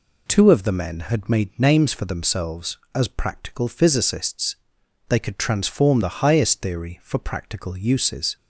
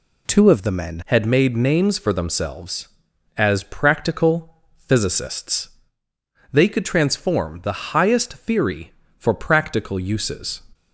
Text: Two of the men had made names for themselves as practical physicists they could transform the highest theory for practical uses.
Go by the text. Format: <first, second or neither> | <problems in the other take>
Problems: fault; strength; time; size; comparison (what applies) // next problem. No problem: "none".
first | changes voice at "had"; from 1.0 s on; 9.6 s long // pauses between "practical" and "physicists"; slight; at 4.5 s; 0.22 s long // pauses between "physicists" and "they"; noticeable; at 5.6 s; 0.84 s long; noticeable in the first